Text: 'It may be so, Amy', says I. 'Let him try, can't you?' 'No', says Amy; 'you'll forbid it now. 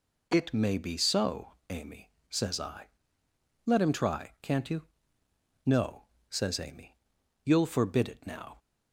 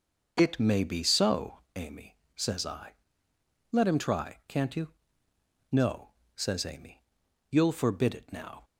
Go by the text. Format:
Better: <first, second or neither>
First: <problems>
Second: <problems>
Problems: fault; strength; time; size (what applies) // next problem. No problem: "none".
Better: first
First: none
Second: starts louder than the rest; noticeable; until 1.6 s; 6 dB